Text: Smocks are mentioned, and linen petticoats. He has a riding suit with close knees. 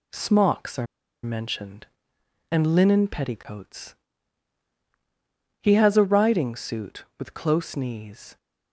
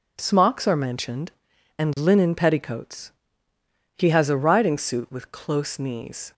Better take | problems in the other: second | pauses between "are" and "mentioned"; at 0.8 s; 0.37 s long

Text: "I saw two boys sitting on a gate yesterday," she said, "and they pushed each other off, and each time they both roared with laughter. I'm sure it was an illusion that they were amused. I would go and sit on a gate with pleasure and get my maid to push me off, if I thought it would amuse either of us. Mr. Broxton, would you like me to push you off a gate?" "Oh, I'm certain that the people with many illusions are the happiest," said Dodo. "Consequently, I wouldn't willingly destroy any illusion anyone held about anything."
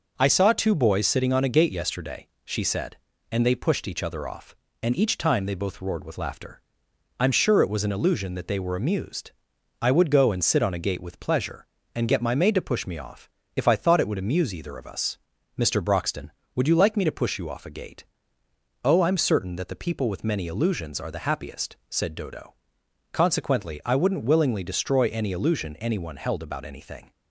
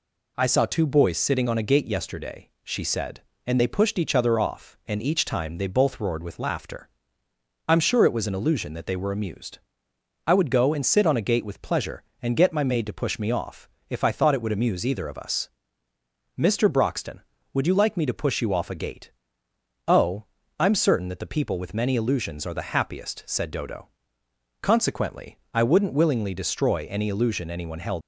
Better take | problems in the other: first | stops before "about anything"; at 28.0 s

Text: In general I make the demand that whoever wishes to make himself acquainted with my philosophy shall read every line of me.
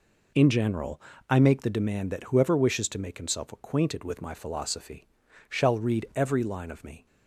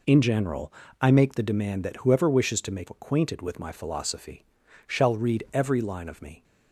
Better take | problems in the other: first | pauses between "general" and "I"; slight; at 0.7 s; 0.28 s long; slight in the first // skips "himself"; at 2.8 s // pauses between "philosophy" and "shall"; at 4.4 s; 0.44 s long; also in the first

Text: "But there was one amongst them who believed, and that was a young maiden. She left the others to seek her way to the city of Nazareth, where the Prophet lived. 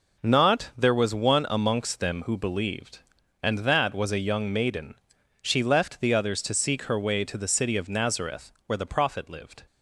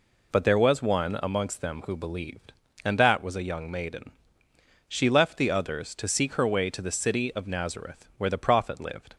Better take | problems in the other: second | says "Not" for "But"; at 0.1 s

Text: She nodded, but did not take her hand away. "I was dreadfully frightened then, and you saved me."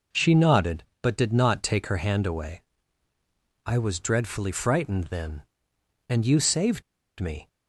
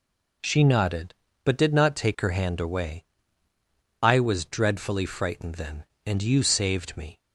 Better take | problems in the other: second | pauses between "saved" and "me"; at 6.8 s; 0.36 s long

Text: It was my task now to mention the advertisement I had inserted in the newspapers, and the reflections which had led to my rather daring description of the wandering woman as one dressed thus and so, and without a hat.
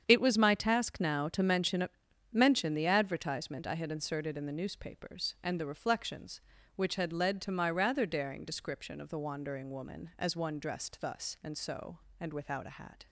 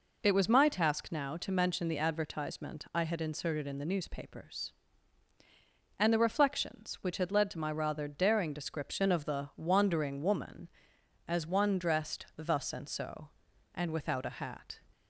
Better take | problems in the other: second | starts louder than the rest; strong; until 1.0 s; 8 dB // says "mention" twice; at 2.3 s

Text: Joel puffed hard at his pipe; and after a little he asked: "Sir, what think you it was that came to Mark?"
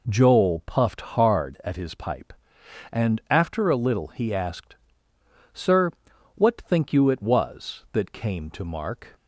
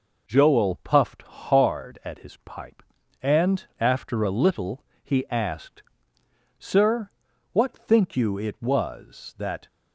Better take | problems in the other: first | pauses between "little" and "he"; slight; at 4.8 s; 0.19 s long // stops before "came to Mark"; at 9.6 s

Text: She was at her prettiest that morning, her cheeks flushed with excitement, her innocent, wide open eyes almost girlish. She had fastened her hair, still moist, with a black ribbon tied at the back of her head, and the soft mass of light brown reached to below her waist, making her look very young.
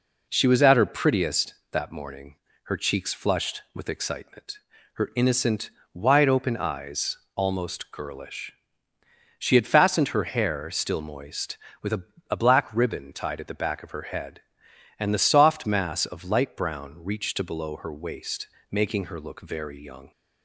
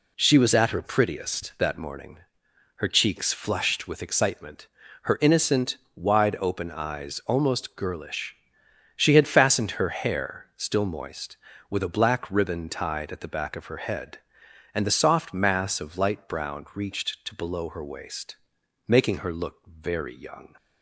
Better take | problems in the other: second | pauses between "eyes" and "almost"; slight; at 7.1 s; 0.18 s long // says "a" twice; at 12.3 s

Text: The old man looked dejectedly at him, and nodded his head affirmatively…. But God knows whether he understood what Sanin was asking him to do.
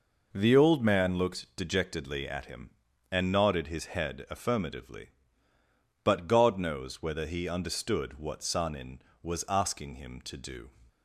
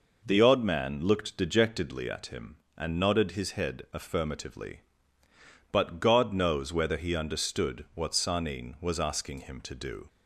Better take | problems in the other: first | says "odd" for "old"; at 0.3 s

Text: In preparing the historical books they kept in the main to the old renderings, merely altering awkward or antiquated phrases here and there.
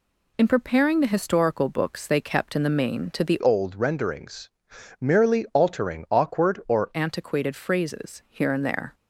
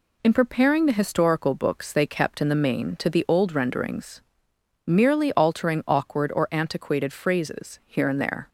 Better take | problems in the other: second | changes voice from "old" to "or"; from 3.4 to 6.9 s; 3.5 s long

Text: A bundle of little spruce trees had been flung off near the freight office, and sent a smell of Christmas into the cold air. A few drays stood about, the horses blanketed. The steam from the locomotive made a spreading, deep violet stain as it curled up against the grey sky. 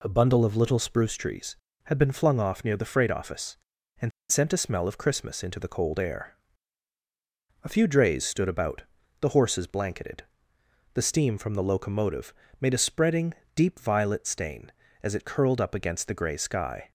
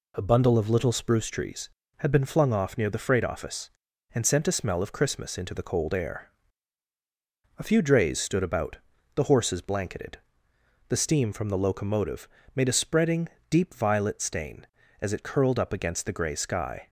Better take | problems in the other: second | pauses between "and" and "sent"; slight; at 4.1 s; 0.19 s long // pauses between "locomotive" and "made"; slight; at 12.3 s; 0.26 s long; slight in the second

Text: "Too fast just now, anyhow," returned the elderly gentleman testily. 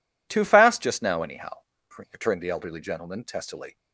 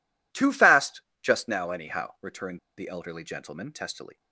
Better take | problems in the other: first | pauses between "fast" and "just"; slight; at 1.0 s; 0.22 s long // pauses between "returned" and "the"; slight; at 2.5 s; 0.19 s long

